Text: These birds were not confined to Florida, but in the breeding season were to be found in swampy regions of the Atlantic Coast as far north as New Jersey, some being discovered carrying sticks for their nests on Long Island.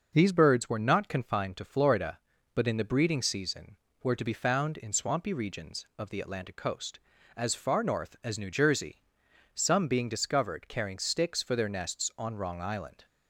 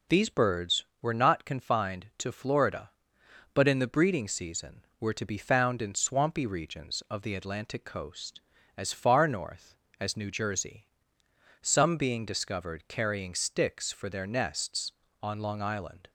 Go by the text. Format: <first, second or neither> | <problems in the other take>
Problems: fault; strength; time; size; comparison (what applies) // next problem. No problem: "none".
second | says "Wrong" for "Long"; at 12.3 s